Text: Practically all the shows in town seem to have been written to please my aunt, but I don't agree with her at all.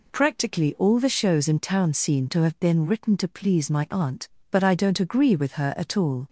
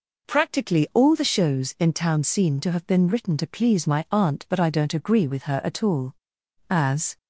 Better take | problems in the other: first | goes on to say "As"; slight; from 6.6 s on; 0.48 s long

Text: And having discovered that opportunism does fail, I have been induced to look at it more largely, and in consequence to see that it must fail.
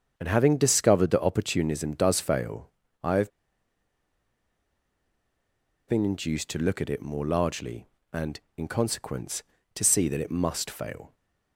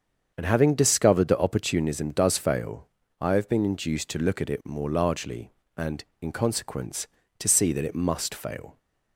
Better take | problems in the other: second | starts louder than the rest; strong; until 1.1 s; 7.5 dB; strong in the second // pauses between "have" and "been"; strong; at 3.3 s; 2.5 s long

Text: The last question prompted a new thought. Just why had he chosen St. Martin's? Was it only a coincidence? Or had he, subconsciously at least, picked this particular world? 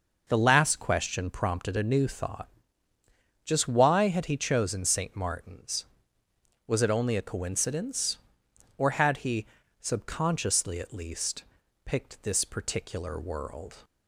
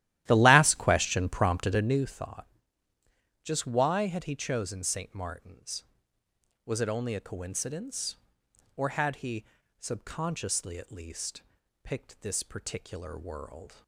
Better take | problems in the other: first | starts louder than the rest; strong; until 2.1 s; 13.5 dB

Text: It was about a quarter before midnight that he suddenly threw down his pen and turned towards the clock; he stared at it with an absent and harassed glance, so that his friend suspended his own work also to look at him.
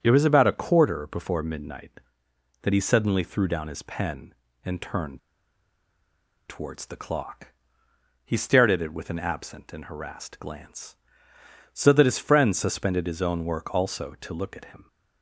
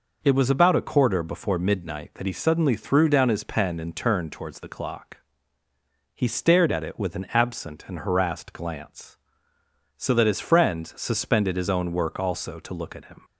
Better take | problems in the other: second | starts louder than the rest; strong; until 1.0 s; 8 dB // pauses between "turned" and "towards"; strong; at 5.1 s; 1.2 s long

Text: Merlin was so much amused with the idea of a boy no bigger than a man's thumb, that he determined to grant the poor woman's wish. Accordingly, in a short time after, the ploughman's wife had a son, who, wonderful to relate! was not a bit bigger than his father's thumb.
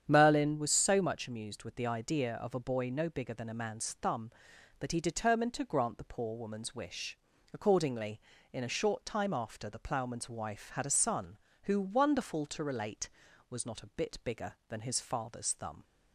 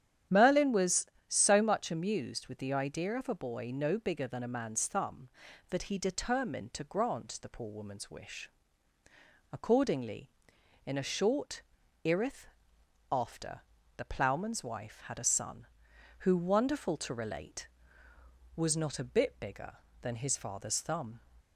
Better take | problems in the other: first | starts louder than the rest; strong; until 1.5 s; 9.5 dB; strong in the first // says "irith" for "time"; at 12.0 s

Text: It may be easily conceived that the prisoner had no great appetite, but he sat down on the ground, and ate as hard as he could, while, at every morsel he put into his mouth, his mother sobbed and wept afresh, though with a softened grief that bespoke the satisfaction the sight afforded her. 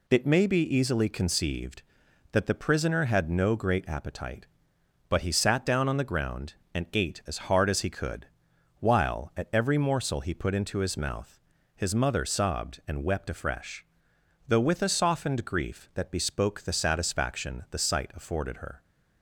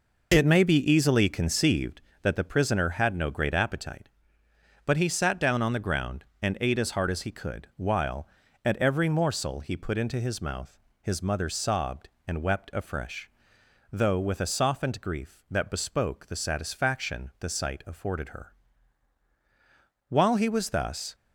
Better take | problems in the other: first | goes on to say "While he was thus"; noticeable; from 20.0 s on; 1.0 s long

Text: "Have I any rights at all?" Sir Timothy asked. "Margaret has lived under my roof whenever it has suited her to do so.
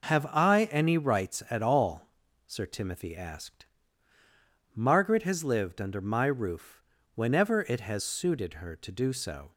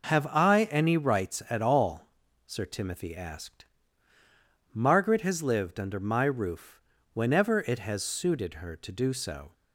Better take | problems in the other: neither | pauses between "roof" and "whenever"; slight; the same in both

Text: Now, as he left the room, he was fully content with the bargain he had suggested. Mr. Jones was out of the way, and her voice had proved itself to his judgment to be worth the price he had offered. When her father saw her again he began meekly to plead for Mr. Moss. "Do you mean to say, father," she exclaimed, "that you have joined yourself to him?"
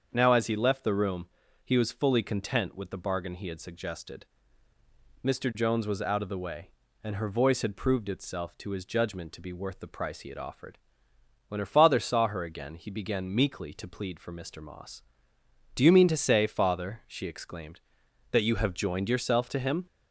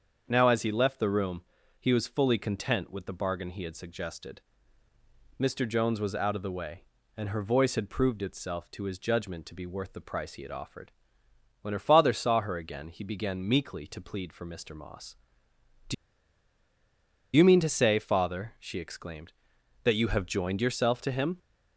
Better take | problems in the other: first | starts louder than the rest; strong; until 1.2 s; 7 dB; strong in the first // pauses between "Do" and "you"; strong; at 15.9 s; 1.4 s long

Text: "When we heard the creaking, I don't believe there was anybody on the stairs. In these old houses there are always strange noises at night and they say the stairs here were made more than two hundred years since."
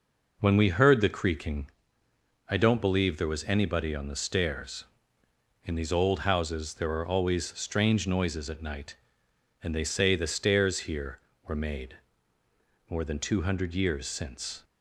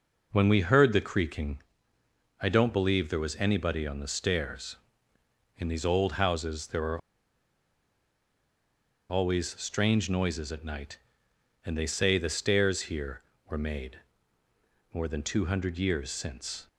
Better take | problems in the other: first | pauses between "are" and "always"; strong; at 6.9 s; 2.0 s long // pauses between "made" and "more"; noticeable; at 13.9 s; 0.94 s long; noticeable in the first

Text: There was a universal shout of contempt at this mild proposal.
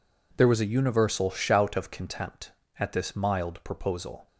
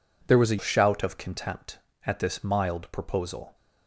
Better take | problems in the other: first | skips "universal"; at 0.5 s

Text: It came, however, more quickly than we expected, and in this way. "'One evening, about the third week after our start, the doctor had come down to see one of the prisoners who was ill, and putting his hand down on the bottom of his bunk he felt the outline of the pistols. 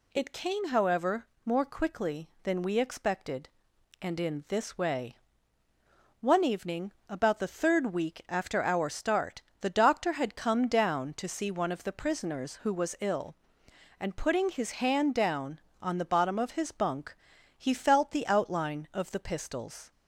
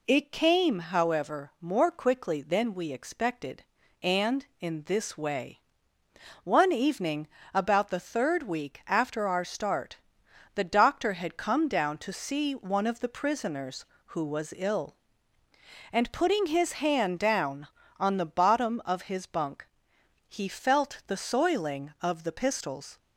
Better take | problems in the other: first | pauses between "bunk" and "he"; noticeable; at 19.6 s; 0.62 s long; also in the first // says "soiling" for "outline"; at 21.1 s

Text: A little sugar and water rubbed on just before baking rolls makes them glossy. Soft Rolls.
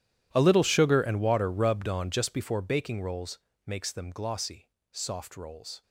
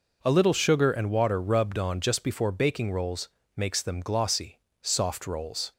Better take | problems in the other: second | gets quieter; strong; throughout; 20 dB // pauses between "rolls" and "makes"; slight; at 3.3 s; 0.26 s long; slight in the second

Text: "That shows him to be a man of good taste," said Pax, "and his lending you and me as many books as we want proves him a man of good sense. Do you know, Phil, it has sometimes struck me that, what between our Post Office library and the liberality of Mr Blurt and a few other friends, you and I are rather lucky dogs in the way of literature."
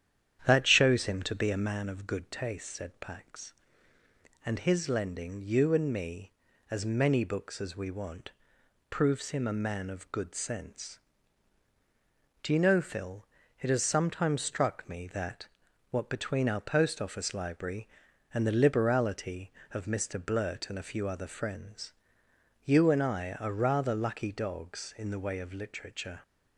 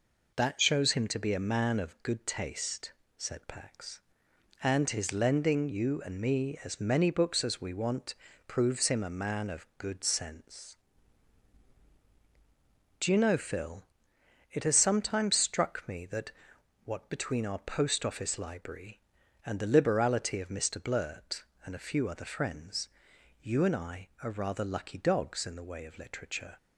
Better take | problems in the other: second | starts louder than the rest; strong; until 1.9 s; 9.5 dB // pauses between "want" and "proves"; noticeable; at 8.3 s; 0.56 s long; slight in the second

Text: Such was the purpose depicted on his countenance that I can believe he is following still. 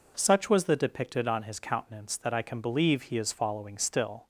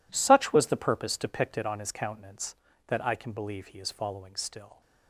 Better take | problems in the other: second | skips "purpose"; at 0.7 s

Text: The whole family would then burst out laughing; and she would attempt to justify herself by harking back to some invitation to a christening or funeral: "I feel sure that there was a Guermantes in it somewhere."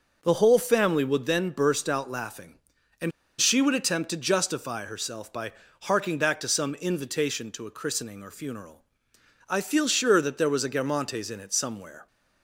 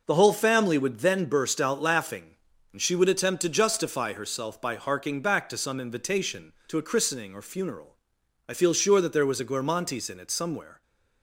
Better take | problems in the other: second | pauses between "and" and "she"; slight; at 3.1 s; 0.29 s long // pauses between "by" and "harking"; slight; at 5.5 s; 0.32 s long

